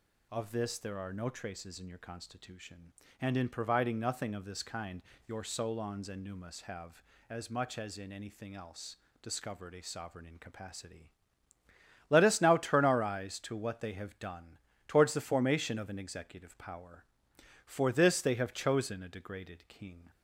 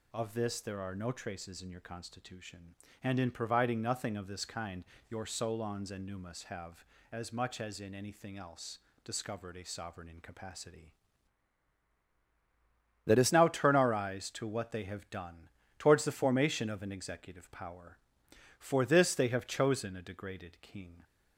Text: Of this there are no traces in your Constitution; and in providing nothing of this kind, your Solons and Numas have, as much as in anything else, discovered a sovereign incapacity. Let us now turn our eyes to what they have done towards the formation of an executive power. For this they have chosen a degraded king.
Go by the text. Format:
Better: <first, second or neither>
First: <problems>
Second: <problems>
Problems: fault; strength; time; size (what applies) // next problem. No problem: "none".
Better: first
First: pauses between "done" and "towards"; slight; at 14.5 s; 0.30 s long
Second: changes voice from "Let" to "us"; from 13.0 to 13.3 s; 0.3 s long // pauses between "done" and "towards"; slight; at 15.4 s; 0.30 s long